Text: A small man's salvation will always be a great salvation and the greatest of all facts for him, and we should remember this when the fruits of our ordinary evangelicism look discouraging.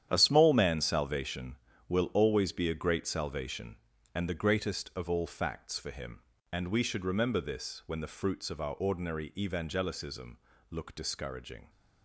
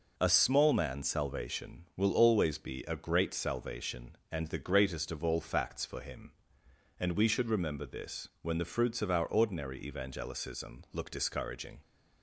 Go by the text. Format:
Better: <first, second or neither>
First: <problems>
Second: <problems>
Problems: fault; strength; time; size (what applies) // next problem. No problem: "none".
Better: second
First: gets quieter; strong; throughout; 12 dB // pauses between "evangelicism" and "look"; slight; at 10.3 s; 0.32 s long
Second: none